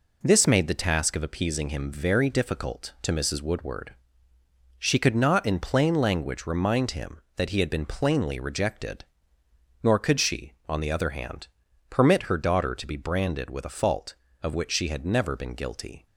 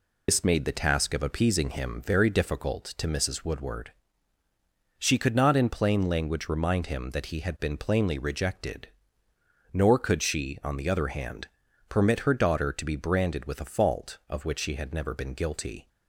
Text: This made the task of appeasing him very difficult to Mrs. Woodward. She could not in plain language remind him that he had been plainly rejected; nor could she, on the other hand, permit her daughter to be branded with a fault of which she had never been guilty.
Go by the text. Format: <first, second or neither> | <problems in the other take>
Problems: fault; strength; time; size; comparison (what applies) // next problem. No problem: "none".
first | loses the start of "This"; at 0.2 s; 95 ms